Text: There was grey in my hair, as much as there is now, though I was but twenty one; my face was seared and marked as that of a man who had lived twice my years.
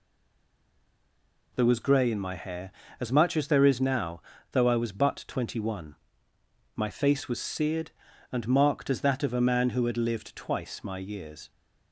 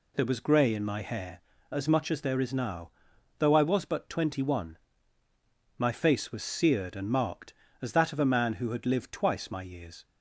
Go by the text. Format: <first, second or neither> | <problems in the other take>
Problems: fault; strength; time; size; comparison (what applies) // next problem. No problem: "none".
second | stays silent before the first word; noticeable; until 1.5 s; 1.5 s long